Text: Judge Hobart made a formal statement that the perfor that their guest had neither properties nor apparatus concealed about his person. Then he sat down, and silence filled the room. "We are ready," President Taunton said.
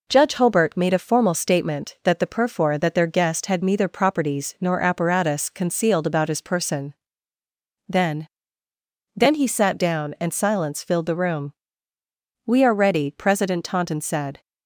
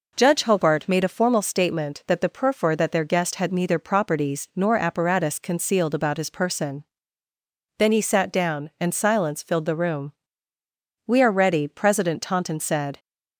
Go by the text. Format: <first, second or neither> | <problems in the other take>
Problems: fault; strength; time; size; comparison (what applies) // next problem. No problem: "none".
second | says "Then" twice; at 9.1 s